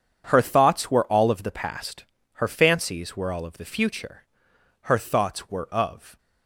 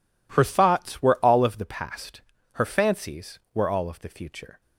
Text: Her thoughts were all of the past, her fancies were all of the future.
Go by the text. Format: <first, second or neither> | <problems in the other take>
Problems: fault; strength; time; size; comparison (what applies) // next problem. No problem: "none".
second | goes on to say "Her thoughts were of"; noticeable; from 4.8 s on; 1.3 s long